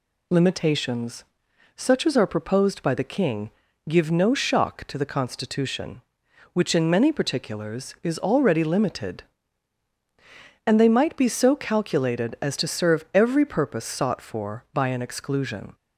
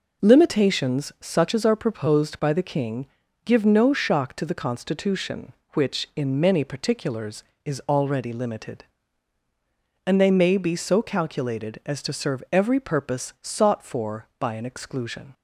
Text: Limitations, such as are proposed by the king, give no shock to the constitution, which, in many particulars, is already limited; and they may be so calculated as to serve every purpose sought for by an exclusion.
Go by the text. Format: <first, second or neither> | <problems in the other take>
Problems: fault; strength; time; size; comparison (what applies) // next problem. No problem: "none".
second | says "might" for "may"; at 10.8 s